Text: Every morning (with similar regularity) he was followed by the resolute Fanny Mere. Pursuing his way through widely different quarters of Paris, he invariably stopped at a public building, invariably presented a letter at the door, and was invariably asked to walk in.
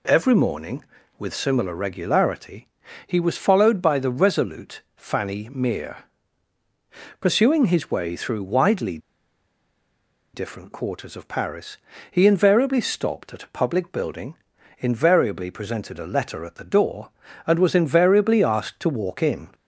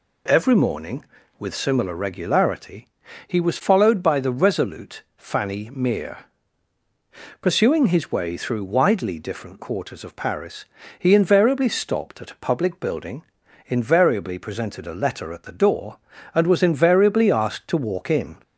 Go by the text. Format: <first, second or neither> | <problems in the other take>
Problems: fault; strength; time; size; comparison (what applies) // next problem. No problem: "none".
second | pauses between "widely" and "different"; strong; at 8.9 s; 1.3 s long